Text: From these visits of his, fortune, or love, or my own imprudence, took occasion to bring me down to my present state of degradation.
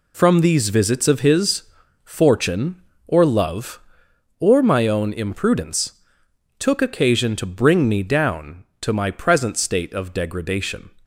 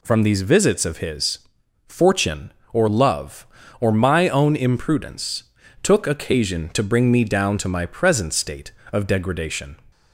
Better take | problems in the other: neither | none

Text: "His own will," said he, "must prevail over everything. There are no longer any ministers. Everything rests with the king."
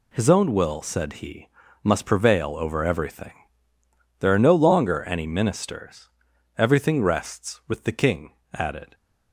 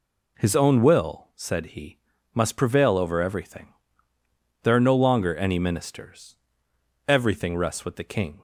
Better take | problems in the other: second | goes on to say "Added"; slight; from 8.5 s on; 0.42 s long

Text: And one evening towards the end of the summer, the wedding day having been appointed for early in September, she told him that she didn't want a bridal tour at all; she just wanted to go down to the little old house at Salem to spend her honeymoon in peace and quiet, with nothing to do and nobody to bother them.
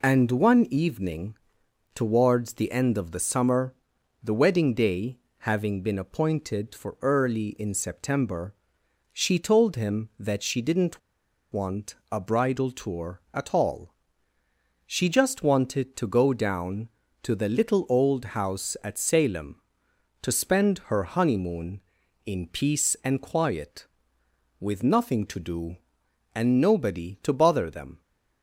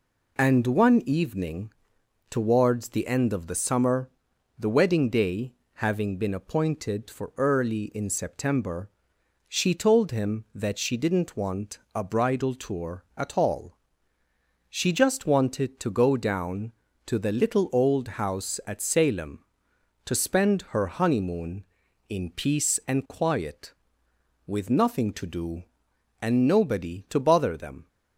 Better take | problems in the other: second | pauses between "evening" and "towards"; noticeable; at 1.3 s; 0.58 s long; noticeable in the second // pauses between "day" and "having"; slight; at 5.1 s; 0.22 s long; slight in the second // pauses between "didn't" and "want"; noticeable; at 10.9 s; 0.52 s long // pauses between "want" and "a"; slight; at 11.9 s; 0.16 s long; slight in the second

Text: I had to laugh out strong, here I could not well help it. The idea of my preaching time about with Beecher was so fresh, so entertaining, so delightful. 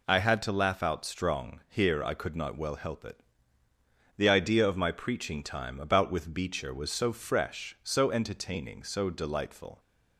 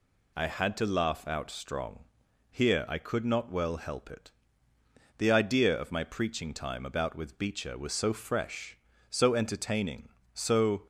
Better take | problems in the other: first | stops before "delightful"; at 10.8 s

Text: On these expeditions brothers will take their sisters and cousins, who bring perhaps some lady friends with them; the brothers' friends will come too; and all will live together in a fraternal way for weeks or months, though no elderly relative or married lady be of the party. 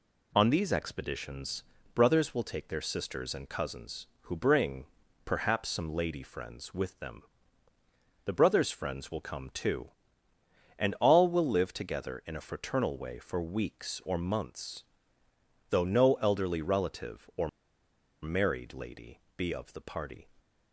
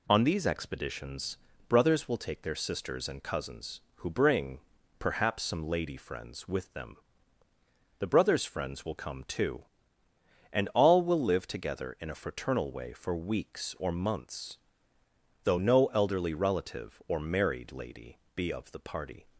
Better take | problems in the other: second | pauses between "expeditions" and "brothers"; slight; at 1.6 s; 0.30 s long; slight in the second // pauses between "bring" and "perhaps"; at 4.8 s; 0.40 s long; also in the second // pauses between "or" and "married"; noticeable; at 17.4 s; 0.72 s long // pauses between "lady" and "be"; slight; at 19.2 s; 0.16 s long; slight in the second

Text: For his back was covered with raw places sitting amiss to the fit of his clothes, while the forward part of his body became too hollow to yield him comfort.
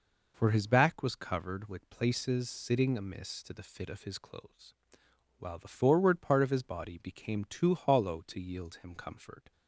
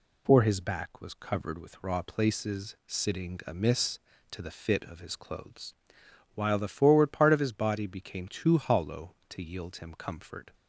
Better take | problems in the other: second | skips "raw"; at 1.8 s

